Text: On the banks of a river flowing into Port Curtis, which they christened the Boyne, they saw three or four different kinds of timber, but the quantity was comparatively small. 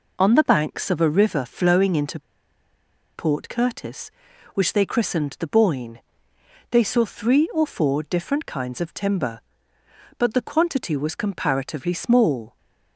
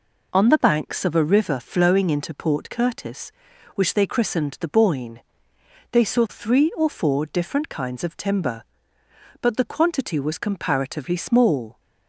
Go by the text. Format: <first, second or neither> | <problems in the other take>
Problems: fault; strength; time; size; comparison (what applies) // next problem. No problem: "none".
second | pauses between "into" and "Port"; noticeable; at 2.1 s; 0.96 s long